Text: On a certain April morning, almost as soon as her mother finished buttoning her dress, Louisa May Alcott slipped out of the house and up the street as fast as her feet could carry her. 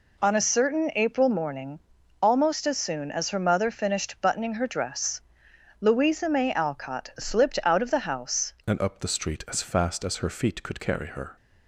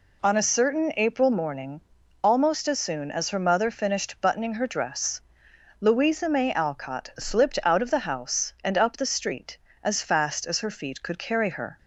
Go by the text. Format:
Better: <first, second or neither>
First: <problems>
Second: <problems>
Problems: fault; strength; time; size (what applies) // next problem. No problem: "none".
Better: second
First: changes voice at "and"; from 8.6 s on; 2.7 s long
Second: none